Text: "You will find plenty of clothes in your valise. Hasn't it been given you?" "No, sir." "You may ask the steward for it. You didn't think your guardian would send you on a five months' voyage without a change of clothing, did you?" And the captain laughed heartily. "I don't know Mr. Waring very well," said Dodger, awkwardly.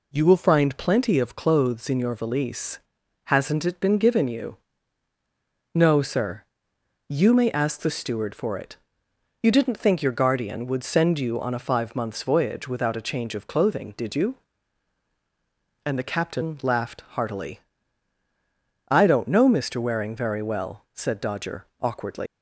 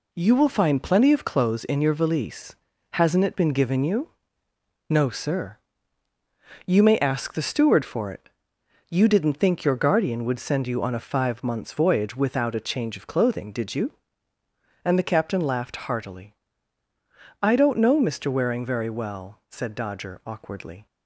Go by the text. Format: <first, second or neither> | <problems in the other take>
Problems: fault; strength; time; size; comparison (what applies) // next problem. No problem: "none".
second | leaves "awkwardly" unfinished; at 22.2 s; 110 ms